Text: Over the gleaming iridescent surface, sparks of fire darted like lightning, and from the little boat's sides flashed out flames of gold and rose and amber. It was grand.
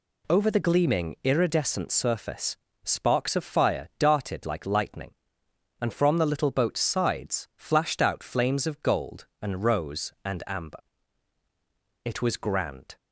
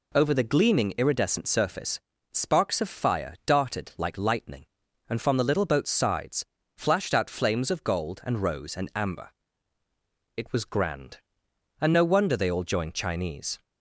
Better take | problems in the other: first | pauses between "sides" and "flashed"; slight; at 6.4 s; 0.32 s long // goes on to say "And no wonder they all joined Chinese"; strong; from 11.8 s on; 1.8 s long

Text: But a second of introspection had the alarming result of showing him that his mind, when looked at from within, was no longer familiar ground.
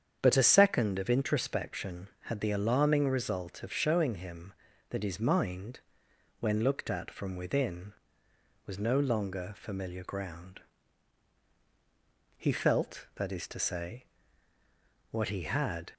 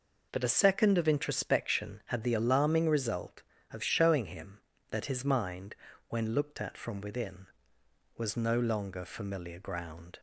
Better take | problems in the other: second | starts louder than the rest; strong; until 1.2 s; 8 dB // goes on to say "He felt that is to say what he had"; strong; from 12.3 s on; 3.5 s long

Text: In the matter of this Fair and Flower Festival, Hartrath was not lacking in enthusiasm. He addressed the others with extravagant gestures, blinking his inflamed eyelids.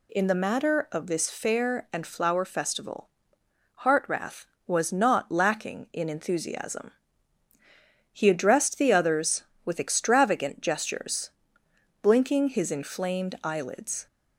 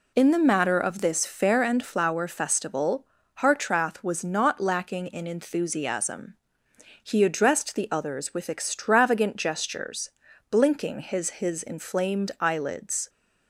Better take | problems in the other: first | says "his" twice; at 11.3 s

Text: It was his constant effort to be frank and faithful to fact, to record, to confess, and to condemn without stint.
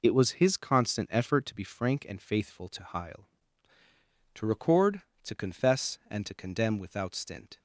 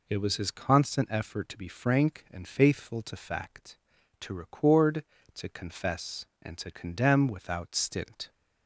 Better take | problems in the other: second | says "heil" for "fact"; at 2.8 s

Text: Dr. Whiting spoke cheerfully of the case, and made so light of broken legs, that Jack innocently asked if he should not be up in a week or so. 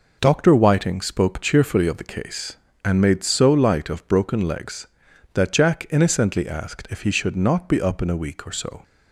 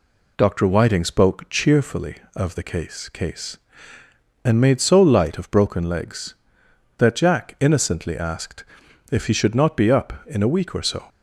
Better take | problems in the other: first | says "case" twice; at 3.0 s // pauses between "asked" and "if"; noticeable; at 8.6 s; 0.46 s long

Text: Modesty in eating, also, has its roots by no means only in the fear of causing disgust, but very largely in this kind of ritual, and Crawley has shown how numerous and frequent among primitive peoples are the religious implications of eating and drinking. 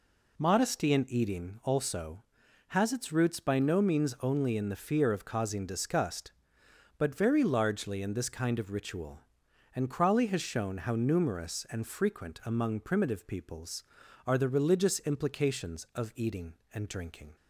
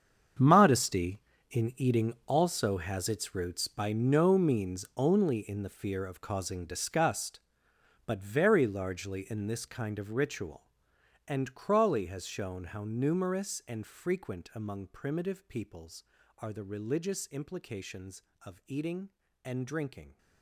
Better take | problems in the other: first | gets quieter; strong; throughout; 15 dB

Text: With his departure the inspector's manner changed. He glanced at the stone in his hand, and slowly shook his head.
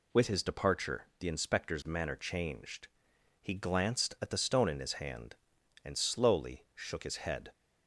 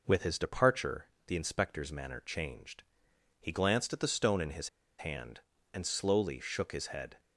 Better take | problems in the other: first | pauses between "departure" and "the"; slight; at 1.0 s; 0.18 s long // pauses between "his" and "hand"; slight; at 4.6 s; 0.29 s long

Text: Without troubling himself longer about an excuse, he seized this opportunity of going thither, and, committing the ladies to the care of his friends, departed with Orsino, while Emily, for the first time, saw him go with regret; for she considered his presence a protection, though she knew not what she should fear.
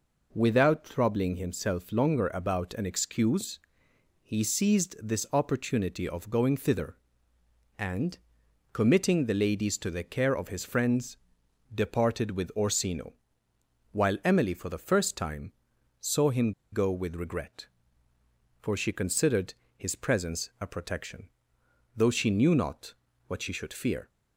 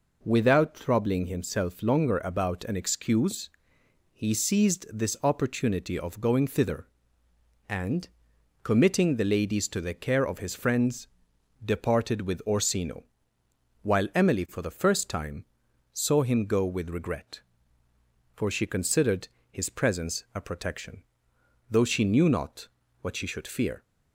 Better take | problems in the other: second | pauses between "him" and "go"; slight; at 16.5 s; 0.19 s long // pauses between "considered" and "his"; slight; at 19.5 s; 0.24 s long; slight in the second // pauses between "not" and "what"; slight; at 22.9 s; 0.32 s long; slight in the second

